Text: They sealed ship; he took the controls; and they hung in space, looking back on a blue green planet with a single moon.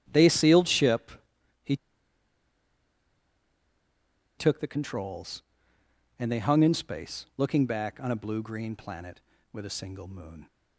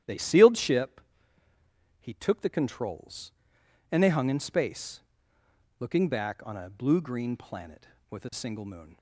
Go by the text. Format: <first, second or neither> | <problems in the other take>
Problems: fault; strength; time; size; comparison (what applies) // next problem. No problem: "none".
second | starts louder than the rest; strong; until 1.6 s; 12 dB; strong in the second // pauses between "he" and "took"; strong; at 1.7 s; 2.6 s long